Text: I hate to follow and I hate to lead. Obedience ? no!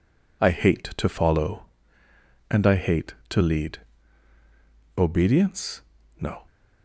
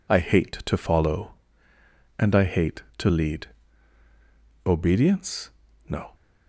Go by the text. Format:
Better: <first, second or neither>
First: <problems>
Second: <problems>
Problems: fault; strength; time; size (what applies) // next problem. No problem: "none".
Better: neither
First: none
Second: none